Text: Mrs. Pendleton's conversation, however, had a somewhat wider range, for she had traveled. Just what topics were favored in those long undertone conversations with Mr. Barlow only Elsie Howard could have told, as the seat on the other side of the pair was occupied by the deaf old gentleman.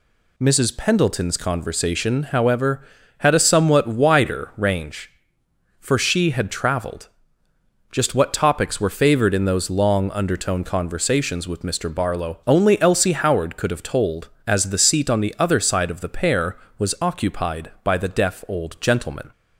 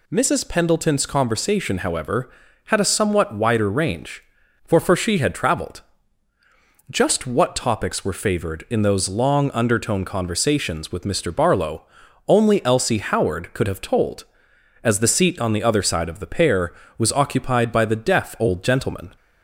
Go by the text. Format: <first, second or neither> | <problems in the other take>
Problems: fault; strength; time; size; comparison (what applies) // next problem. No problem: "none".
first | says "for" twice; at 4.7 s // pauses between "Barlow" and "only"; noticeable; at 11.8 s; 0.46 s long